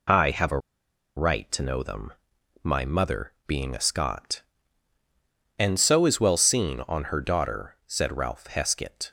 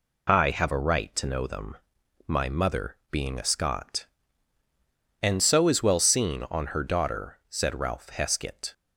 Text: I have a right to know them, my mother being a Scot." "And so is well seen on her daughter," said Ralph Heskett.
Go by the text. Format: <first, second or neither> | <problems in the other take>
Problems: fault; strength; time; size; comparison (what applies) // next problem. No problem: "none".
second | pauses between "a" and "right"; noticeable; at 0.5 s; 0.57 s long